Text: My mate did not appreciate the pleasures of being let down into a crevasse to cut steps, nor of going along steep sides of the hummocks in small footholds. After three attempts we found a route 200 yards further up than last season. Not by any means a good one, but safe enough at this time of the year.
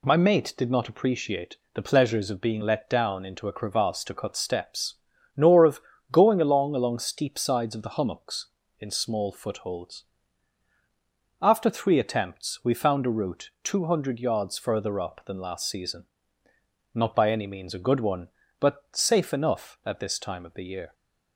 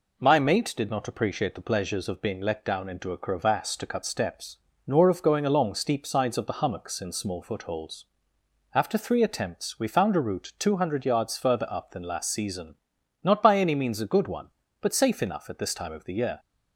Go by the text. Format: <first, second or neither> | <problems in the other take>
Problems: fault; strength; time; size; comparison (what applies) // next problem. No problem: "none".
second | pauses between "appreciate" and "the"; slight; at 1.5 s; 0.16 s long // pauses between "of" and "going"; slight; at 5.7 s; 0.30 s long // says "along" twice; at 6.7 s